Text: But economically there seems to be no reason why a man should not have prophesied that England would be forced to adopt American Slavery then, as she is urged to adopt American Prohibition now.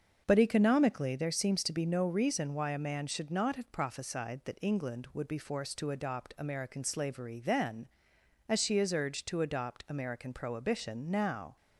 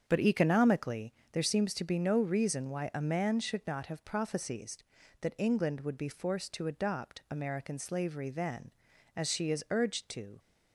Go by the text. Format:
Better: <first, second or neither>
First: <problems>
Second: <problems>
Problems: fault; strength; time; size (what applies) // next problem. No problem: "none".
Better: first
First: starts louder than the rest; until 1.2 s; 6.5 dB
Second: starts louder than the rest; strong; until 1.0 s; 7.5 dB // pauses between "economically" and "there"; slight; at 1.1 s; 0.20 s long // stops before "adopt American Prohibition now"; at 10.3 s